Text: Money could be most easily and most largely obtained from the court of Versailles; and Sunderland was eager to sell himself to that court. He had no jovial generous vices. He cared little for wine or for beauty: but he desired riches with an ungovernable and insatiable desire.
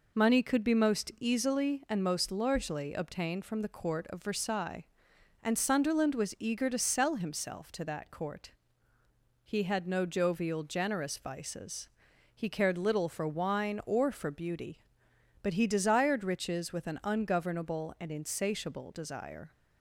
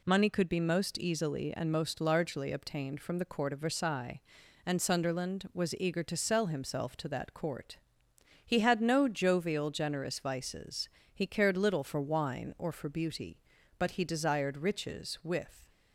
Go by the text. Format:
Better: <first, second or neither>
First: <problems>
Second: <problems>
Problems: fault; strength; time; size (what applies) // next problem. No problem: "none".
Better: first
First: none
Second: stops before "an ungovernable and insatiable desire"; at 15.6 s